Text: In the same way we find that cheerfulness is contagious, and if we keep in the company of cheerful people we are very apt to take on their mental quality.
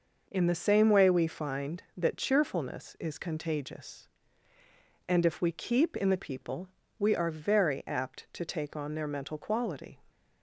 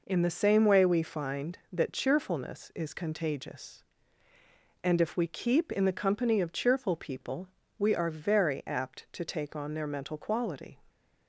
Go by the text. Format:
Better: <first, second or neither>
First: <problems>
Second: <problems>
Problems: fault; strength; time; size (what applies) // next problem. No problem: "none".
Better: second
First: skips "company of cheerful"; at 6.1 s // pauses between "people" and "we"; slight; at 6.6 s; 0.30 s long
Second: pauses between "people" and "we"; slight; at 7.4 s; 0.30 s long